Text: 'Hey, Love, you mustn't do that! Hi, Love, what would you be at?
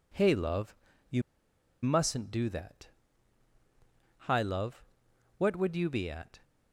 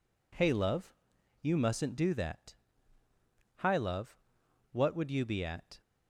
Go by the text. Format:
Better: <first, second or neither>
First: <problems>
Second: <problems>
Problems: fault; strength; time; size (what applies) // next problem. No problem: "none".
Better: second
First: pauses between "you" and "mustn't"; noticeable; at 1.2 s; 0.61 s long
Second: none